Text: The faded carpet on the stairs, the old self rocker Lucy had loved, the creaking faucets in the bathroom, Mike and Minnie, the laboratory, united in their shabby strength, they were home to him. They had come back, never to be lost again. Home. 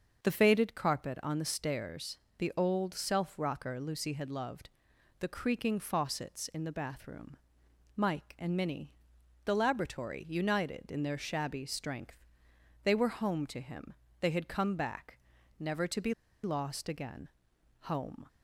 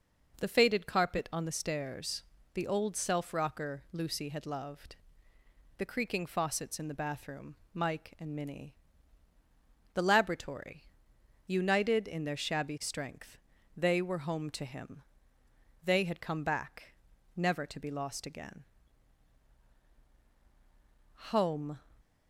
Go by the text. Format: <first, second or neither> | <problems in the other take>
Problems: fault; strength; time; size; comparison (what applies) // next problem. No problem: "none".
second | starts louder than the rest; until 1.2 s; 6.5 dB // pauses between "be" and "lost"; slight; at 16.1 s; 0.30 s long